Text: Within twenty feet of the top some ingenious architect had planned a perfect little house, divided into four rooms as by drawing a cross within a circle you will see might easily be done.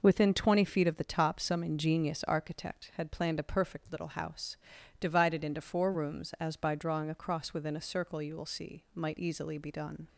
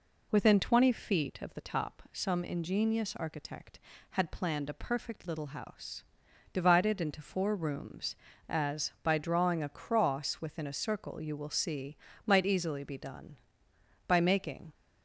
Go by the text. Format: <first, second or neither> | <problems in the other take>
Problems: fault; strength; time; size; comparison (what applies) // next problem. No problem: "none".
first | pauses between "see" and "might"; slight; at 11.9 s; 0.30 s long // goes on to say "By making"; noticeable; from 14.0 s on; 0.66 s long